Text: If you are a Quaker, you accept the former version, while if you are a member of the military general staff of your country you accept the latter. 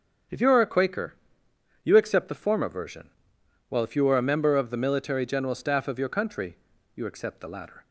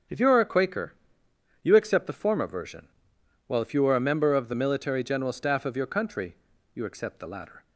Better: neither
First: starts louder than the rest; strong; until 2.0 s; 8.5 dB // pauses between "country" and "you"; at 6.5 s; 0.38 s long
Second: starts louder than the rest; strong; until 1.7 s; 8.5 dB // pauses between "country" and "you"; at 6.3 s; 0.38 s long

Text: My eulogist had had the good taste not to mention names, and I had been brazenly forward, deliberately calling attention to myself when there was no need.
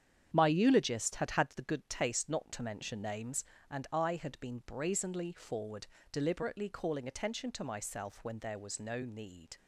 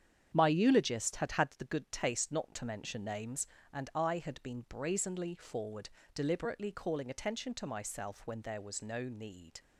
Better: neither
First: starts louder than the rest; strong; until 1.3 s; 8.5 dB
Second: starts louder than the rest; strong; until 1.3 s; 8.5 dB

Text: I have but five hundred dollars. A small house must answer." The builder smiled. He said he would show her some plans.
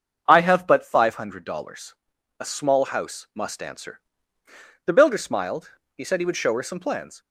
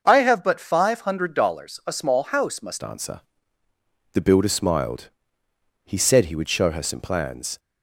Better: first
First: starts louder than the rest; until 1.2 s; 6.5 dB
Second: starts louder than the rest; noticeable; until 1.0 s; 6 dB // changes voice at "answer"; from 2.8 s on; 4.7 s long

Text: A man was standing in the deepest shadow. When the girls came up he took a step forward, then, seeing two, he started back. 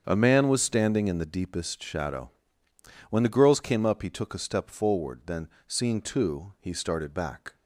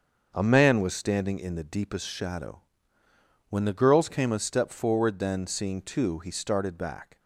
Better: first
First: starts louder than the rest; strong; until 1.1 s; 7.5 dB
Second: starts louder than the rest; until 1.3 s; 6.5 dB // skips "up he took"; at 4.3 s

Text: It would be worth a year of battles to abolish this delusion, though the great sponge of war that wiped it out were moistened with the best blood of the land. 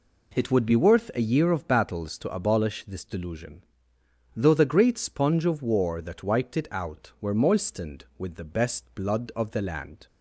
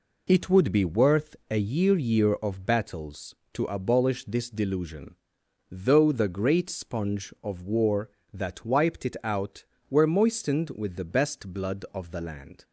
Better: first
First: none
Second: says "year" twice; at 1.9 s

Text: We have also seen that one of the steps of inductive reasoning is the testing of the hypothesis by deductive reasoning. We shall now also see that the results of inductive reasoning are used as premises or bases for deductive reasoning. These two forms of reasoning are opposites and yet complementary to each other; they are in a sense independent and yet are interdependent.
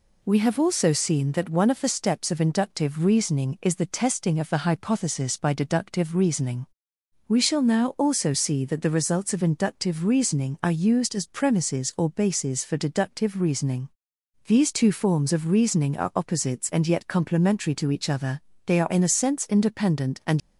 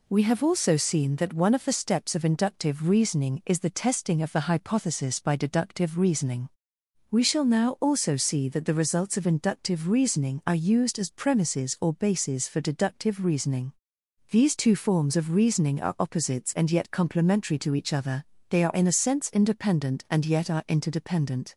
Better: second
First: stops before "yet are interdependent"; at 20.4 s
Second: none

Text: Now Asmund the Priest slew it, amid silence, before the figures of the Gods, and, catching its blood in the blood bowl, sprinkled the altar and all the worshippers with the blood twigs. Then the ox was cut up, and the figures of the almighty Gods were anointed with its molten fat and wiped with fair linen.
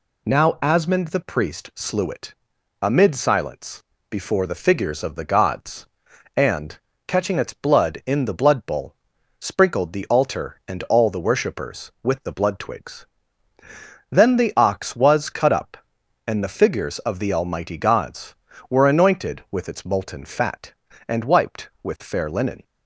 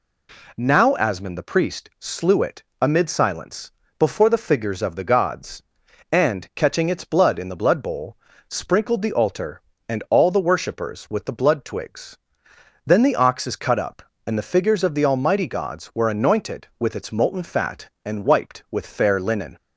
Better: first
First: none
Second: says "is" for "was"; at 13.4 s

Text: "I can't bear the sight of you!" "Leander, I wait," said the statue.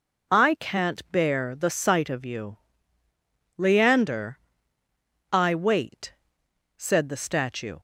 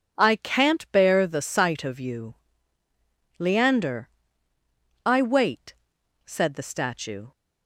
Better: neither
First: none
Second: none

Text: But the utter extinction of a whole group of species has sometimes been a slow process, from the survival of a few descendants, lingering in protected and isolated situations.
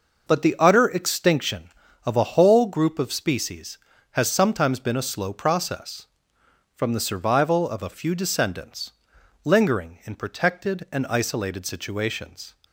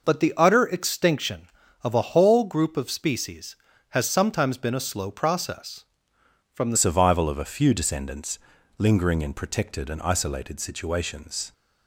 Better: first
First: none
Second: changes voice at "survival"; from 6.7 s on; 4.8 s long

